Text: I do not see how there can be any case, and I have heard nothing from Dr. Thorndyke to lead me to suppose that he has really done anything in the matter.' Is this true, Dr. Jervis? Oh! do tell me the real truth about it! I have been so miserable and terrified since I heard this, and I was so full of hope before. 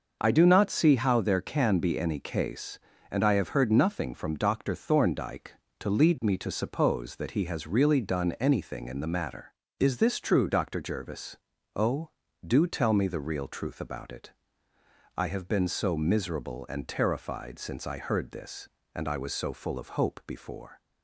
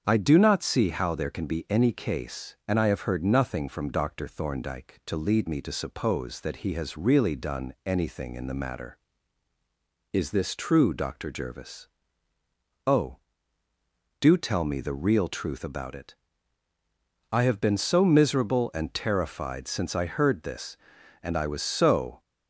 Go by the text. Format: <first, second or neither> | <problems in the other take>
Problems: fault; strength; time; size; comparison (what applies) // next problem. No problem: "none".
first | starts louder than the rest; strong; until 1.0 s; 7 dB // stops before "full of hope before"; at 22.1 s